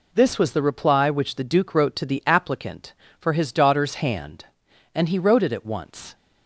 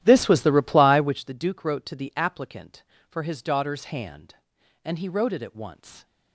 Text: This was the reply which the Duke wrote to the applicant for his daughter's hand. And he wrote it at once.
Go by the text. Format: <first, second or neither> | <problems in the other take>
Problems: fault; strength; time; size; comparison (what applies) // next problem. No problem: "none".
first | starts louder than the rest; strong; until 1.2 s; 12.5 dB